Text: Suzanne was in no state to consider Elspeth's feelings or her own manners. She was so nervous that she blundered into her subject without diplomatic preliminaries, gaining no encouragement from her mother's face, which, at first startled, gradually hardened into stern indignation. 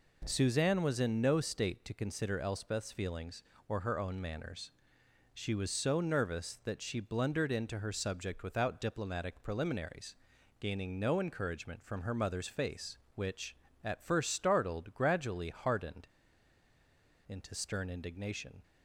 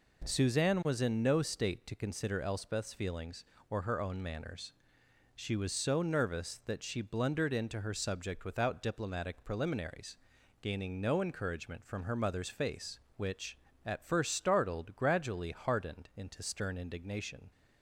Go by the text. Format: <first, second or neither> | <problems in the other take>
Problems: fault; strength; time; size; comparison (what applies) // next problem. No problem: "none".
second | pauses between "hardened" and "into"; at 16.0 s; 1.2 s long